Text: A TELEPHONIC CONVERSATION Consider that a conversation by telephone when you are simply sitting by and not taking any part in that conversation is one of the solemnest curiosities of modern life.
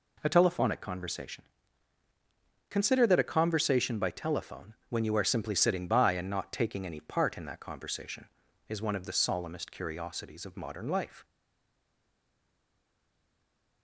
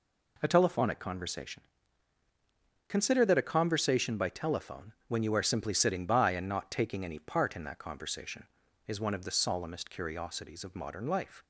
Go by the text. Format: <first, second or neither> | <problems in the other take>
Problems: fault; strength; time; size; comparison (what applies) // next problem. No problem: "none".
second | pauses between "CONVERSATION" and "Consider"; at 1.4 s; 1.2 s long; also in the second // stays silent after the last word; strong; from 11.2 s on; 2.6 s long